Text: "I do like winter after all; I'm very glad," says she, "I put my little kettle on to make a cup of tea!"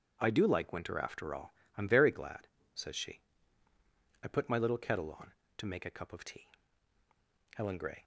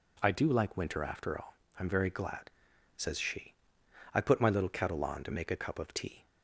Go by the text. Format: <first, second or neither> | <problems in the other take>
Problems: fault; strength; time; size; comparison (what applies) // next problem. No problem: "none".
second | starts louder than the rest; strong; until 1.2 s; 7.5 dB // goes on to say "HELEN GRAY"; slight; from 7.5 s on; 0.48 s long